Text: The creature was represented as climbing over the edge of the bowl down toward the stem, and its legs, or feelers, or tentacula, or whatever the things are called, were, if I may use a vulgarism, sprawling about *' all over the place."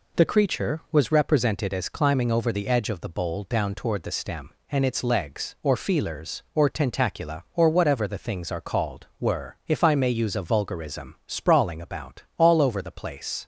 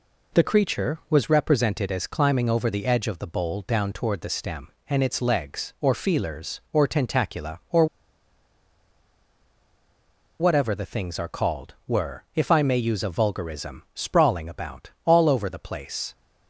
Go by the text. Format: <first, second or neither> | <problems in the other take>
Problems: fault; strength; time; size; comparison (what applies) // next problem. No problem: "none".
first | pauses between "or" and "whatever"; strong; at 7.8 s; 2.5 s long